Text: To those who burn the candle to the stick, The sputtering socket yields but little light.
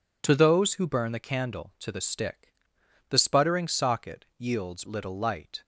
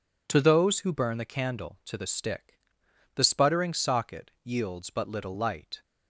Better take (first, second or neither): second